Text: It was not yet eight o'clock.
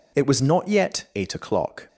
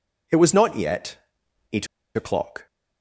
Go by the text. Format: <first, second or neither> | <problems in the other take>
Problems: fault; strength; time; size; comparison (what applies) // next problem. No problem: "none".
first | pauses between "yet" and "eight"; noticeable; at 1.1 s; 0.56 s long // pauses between "eight" and "o'clock"; slight; at 1.8 s; 0.29 s long